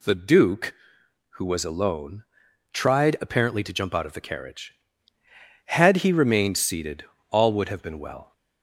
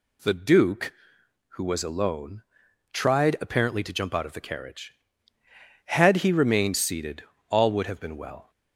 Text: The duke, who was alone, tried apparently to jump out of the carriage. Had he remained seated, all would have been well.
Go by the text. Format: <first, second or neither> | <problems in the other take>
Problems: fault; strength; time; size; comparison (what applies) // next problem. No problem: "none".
neither | none